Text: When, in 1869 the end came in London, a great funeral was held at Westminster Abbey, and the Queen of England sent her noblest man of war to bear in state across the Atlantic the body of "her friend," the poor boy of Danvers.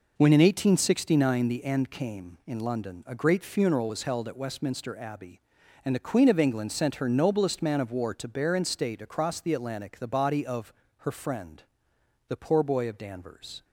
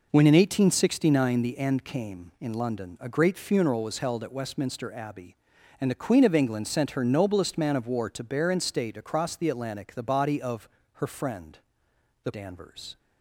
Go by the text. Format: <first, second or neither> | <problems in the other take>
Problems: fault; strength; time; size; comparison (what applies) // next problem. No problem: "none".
first | pauses between "of" and "her"; slight; at 10.6 s; 0.26 s long; slight in the first // skips "poor boy of"; at 12.3 s